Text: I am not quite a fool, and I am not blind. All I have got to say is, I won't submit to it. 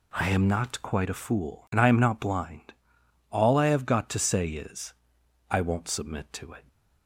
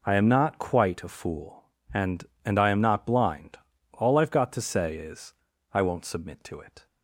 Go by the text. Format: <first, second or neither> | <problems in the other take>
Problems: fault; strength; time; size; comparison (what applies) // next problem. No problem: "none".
first | says "and" twice; at 2.4 s